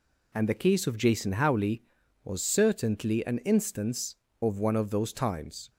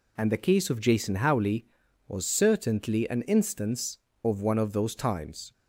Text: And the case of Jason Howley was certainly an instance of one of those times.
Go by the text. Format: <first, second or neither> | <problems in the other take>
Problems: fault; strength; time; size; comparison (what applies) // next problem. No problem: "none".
neither | none